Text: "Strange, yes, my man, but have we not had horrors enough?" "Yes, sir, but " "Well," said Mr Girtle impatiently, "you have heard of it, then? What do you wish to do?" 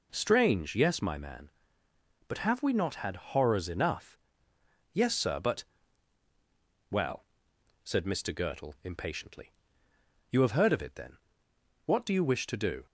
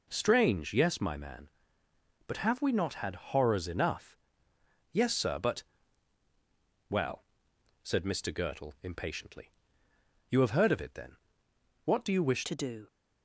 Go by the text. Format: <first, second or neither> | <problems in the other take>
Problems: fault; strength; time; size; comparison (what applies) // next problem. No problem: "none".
first | changes voice at "to"; from 12.4 s on; 0.4 s long